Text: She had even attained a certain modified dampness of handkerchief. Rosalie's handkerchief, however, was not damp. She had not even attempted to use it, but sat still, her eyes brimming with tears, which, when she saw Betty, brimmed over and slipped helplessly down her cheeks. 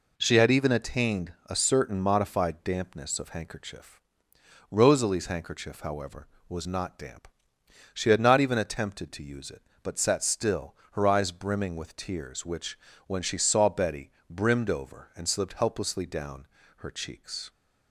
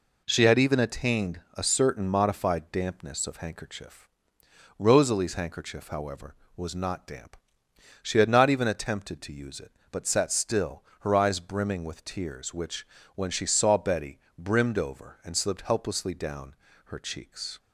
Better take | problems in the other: neither | pauses between "down" and "her"; slight; the same in both

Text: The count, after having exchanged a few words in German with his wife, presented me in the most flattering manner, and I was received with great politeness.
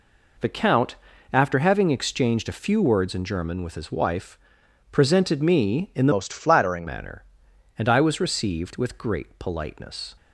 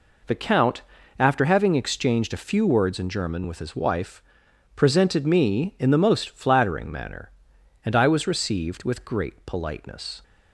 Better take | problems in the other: second | changes voice from "most" to "flattering"; from 6.1 to 6.8 s; 0.7 s long

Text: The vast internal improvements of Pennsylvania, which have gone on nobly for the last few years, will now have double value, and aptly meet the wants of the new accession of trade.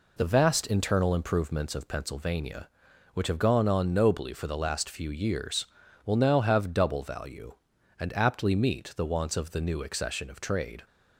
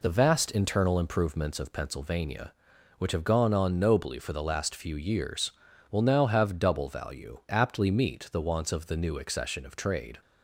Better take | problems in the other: first | skips "and"; at 7.4 s

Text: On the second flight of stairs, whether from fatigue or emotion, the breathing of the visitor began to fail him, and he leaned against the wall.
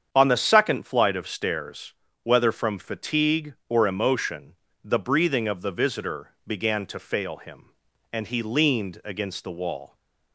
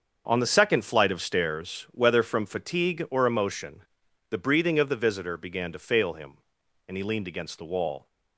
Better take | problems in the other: neither | starts louder than the rest; the same in both

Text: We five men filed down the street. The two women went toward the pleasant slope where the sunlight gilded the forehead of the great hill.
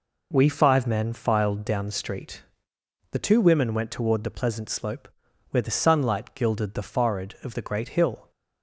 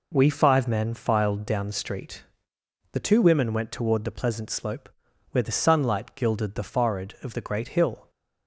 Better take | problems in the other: neither | pauses between "slope" and "where"; the same in both

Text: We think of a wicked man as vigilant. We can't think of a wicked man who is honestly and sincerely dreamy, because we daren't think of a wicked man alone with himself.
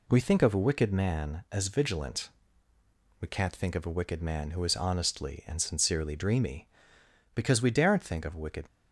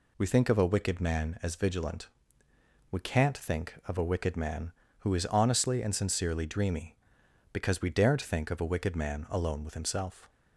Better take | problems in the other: second | stops before "man alone with himself"; at 8.6 s

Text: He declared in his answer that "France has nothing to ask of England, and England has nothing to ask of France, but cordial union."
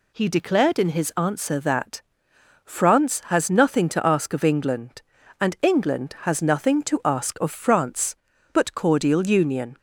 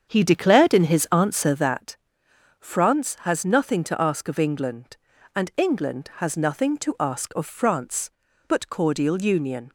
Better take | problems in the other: first | starts louder than the rest; strong; until 1.8 s; 7.5 dB // pauses between "that" and "France"; noticeable; at 1.9 s; 0.64 s long; noticeable in the first

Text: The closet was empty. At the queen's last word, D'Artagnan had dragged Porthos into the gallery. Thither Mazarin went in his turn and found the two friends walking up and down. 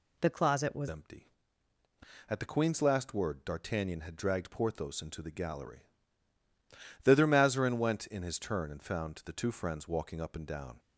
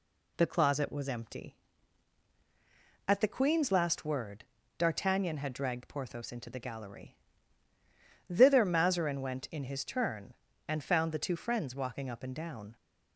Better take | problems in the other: second | changes voice at "empty"; from 0.8 s on; 9.9 s long

